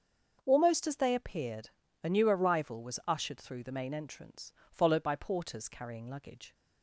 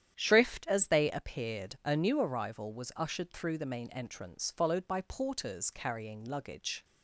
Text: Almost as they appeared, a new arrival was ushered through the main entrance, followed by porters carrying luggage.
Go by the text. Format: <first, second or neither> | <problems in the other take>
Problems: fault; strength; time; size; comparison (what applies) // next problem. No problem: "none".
first | starts louder than the rest; strong; until 1.1 s; 10 dB; also in the first // says "Shrift" for "Almost"; at 0.1 s